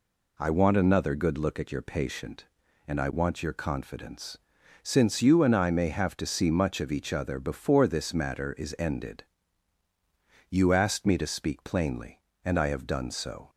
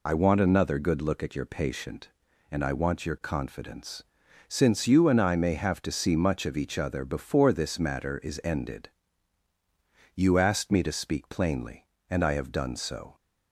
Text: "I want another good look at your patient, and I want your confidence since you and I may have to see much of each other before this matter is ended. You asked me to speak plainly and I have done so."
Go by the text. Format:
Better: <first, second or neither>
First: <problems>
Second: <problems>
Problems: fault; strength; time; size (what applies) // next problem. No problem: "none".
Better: first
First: pauses between "confidence" and "since"; noticeable; at 4.3 s; 0.46 s long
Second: loses the start of "I"; at 0.0 s; 30 ms // pauses between "confidence" and "since"; noticeable; at 4.0 s; 0.46 s long